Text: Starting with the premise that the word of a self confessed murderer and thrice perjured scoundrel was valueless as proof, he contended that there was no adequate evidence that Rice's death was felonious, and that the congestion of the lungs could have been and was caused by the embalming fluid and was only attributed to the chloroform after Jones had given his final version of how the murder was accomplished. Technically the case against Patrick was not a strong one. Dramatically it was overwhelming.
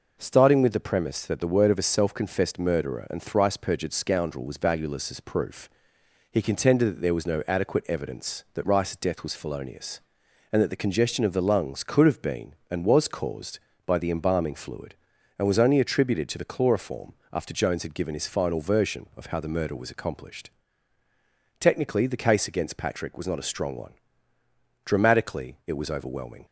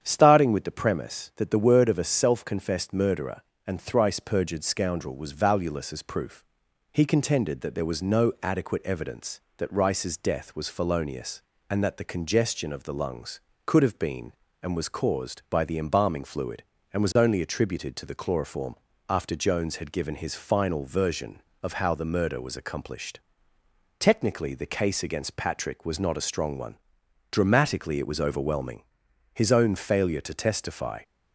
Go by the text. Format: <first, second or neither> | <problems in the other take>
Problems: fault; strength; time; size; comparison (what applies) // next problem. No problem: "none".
first | starts louder than the rest; strong; until 1.0 s; 8.5 dB // pauses between "chloroform" and "after"; slight; at 18.7 s; 0.32 s long; slight in the first // goes on to say "His own failure to testify"; strong; from 29.3 s on; 1.6 s long